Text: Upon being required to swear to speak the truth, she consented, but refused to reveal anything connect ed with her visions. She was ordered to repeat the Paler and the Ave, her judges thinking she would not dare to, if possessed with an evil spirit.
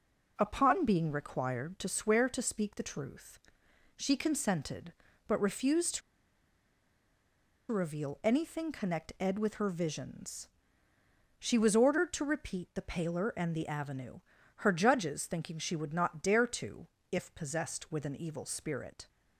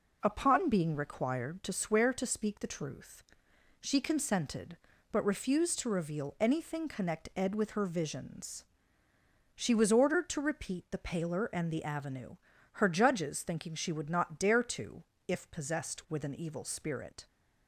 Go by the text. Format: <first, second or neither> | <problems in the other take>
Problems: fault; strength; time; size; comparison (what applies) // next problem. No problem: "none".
second | pauses between "to" and "reveal"; strong; at 6.0 s; 1.7 s long